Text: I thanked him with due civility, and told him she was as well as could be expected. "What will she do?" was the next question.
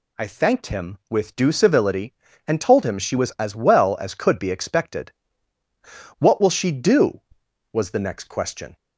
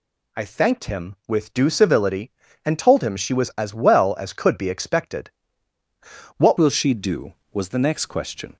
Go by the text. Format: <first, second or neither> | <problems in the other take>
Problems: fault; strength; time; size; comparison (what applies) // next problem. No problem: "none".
first | changes voice at "will"; from 6.5 s on; 2.0 s long